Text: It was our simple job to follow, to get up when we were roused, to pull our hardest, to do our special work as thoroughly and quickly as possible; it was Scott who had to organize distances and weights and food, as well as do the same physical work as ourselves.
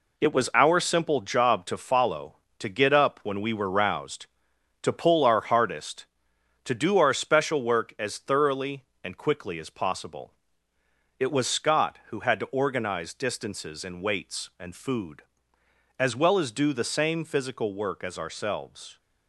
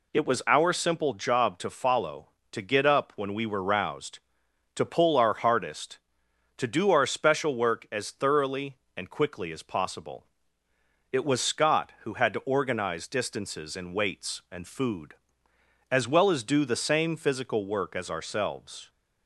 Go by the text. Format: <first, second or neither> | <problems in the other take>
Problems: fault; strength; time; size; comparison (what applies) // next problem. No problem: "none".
second | gets quieter; strong; throughout; 7 dB